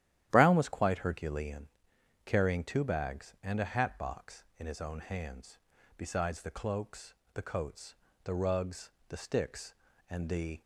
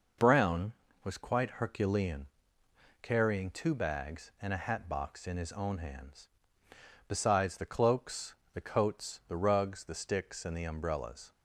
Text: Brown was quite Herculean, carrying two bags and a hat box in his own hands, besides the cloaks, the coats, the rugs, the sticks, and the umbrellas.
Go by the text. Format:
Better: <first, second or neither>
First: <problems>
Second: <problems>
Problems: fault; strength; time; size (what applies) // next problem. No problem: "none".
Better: second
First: starts louder than the rest; strong; until 1.3 s; 12 dB // stops before "umbrellas"; at 10.6 s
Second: none